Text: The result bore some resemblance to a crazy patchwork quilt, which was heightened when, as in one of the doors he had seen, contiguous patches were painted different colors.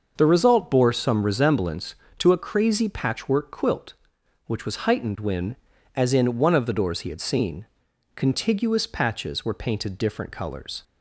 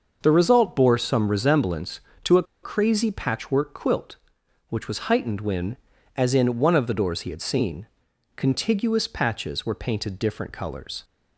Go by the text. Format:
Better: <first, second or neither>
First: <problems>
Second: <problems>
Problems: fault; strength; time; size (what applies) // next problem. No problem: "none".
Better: first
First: starts louder than the rest; until 1.1 s; 6 dB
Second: starts louder than the rest; until 1.2 s; 6 dB // pauses between "a" and "crazy"; slight; at 2.4 s; 0.20 s long